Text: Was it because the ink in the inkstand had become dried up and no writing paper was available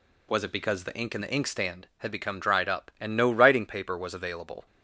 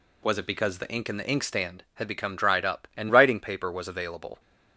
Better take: first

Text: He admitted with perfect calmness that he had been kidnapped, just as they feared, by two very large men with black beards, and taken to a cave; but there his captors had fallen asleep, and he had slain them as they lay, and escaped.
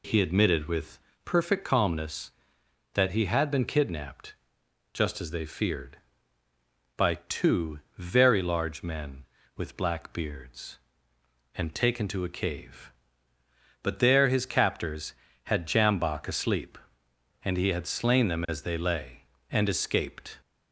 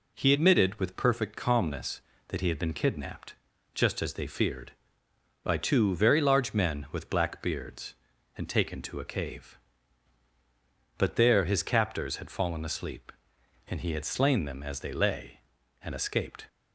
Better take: second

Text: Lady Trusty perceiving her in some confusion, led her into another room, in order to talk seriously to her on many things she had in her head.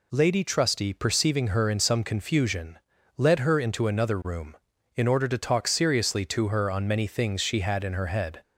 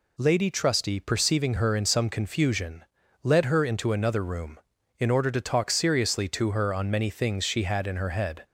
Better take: neither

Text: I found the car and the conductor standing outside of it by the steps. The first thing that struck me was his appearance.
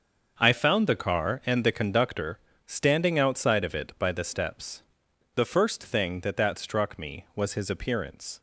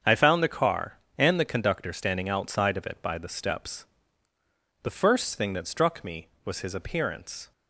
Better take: second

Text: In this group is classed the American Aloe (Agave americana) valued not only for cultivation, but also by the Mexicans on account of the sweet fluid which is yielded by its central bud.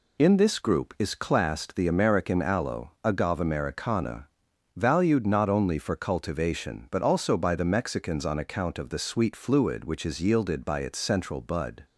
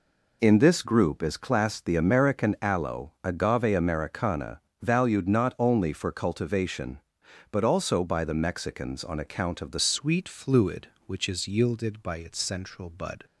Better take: first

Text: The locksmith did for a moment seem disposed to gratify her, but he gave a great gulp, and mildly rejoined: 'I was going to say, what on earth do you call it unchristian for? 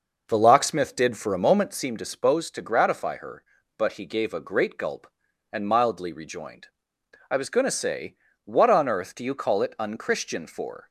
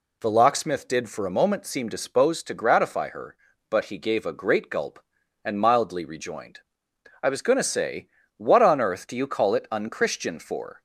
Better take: second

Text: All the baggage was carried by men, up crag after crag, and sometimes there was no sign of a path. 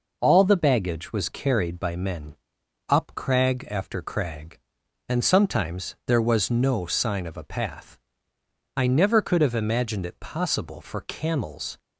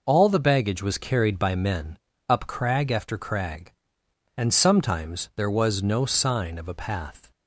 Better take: second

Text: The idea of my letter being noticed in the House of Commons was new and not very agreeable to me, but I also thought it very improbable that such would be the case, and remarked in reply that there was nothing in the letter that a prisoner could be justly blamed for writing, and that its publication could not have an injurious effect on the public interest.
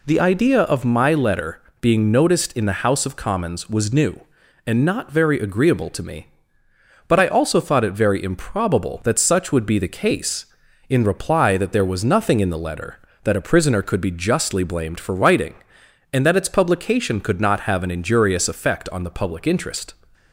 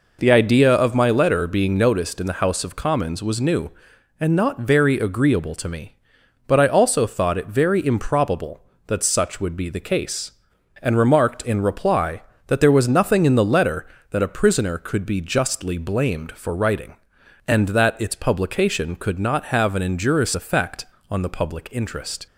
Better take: second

